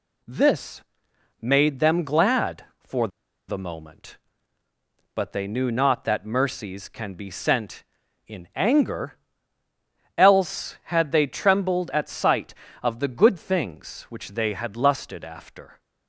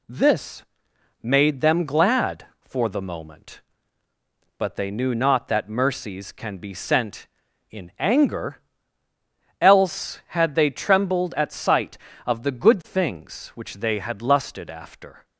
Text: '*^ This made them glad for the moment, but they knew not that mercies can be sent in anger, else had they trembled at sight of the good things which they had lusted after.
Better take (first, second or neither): second